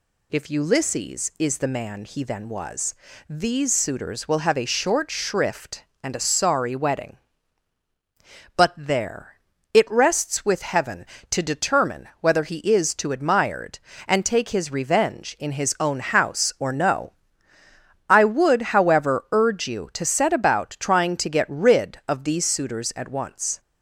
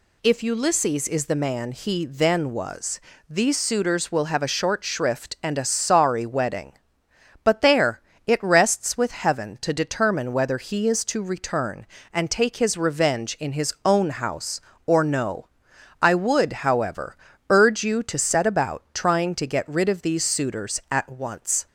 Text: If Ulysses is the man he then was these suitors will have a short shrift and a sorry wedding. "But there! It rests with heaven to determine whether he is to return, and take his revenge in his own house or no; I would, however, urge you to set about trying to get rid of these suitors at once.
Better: second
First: pauses between "was" and "these"; slight; at 2.9 s; 0.34 s long // says "admired" for "return"; at 13.1 s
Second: pauses between "was" and "these"; slight; at 2.9 s; 0.30 s long

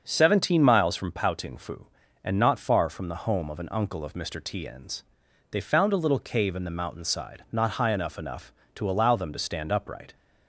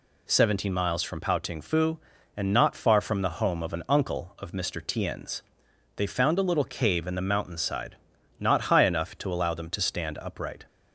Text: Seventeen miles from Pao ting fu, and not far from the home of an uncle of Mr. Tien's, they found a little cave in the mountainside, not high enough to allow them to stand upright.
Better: second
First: starts louder than the rest; until 1.0 s; 6.5 dB // says "enough" twice; at 8.1 s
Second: none

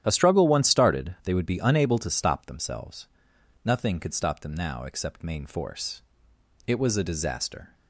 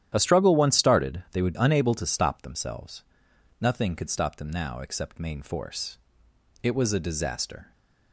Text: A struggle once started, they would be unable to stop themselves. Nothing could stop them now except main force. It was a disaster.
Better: first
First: starts louder than the rest; strong; until 1.0 s; 11 dB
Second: starts louder than the rest; strong; until 1.1 s; 11 dB // skips "be"; at 1.5 s

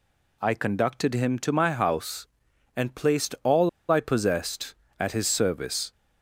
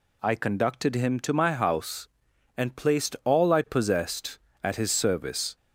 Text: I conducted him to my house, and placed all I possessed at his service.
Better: second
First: pauses between "all" and "I"; slight; at 3.6 s; 0.22 s long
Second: none

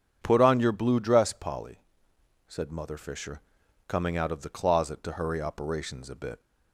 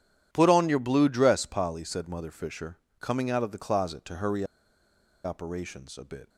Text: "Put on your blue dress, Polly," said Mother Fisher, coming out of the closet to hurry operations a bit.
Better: first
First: none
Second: pauses between "hurry" and "operations"; noticeable; at 4.4 s; 0.79 s long

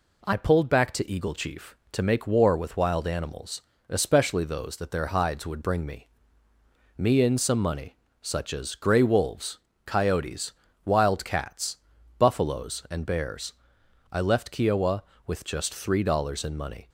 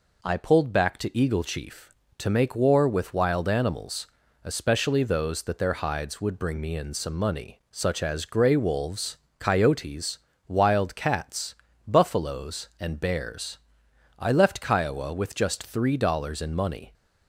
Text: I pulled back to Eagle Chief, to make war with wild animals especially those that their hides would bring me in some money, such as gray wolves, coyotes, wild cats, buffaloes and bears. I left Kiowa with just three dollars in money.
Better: second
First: pauses between "animals" and "especially"; slight; at 3.6 s; 0.28 s long // says "me" twice; at 6.9 s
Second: pauses between "animals" and "especially"; at 4.0 s; 0.38 s long

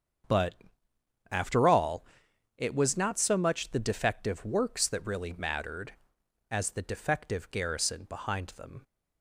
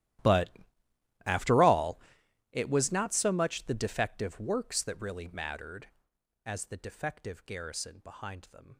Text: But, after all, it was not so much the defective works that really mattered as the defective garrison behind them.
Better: first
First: starts louder than the rest; strong; until 2.0 s; 7.5 dB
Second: gets quieter; strong; throughout; 24 dB // starts louder than the rest; strong; until 1.9 s; 13.5 dB

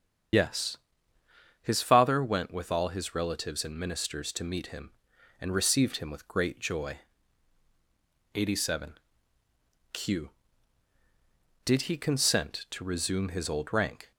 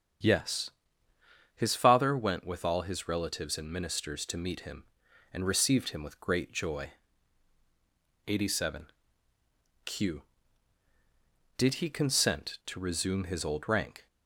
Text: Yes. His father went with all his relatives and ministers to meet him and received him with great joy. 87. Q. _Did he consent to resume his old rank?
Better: second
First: loses the start of "Yes"; at 0.3 s; 60 ms // starts louder than the rest; strong; until 2.1 s; 8 dB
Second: starts louder than the rest; strong; until 2.0 s; 8 dB

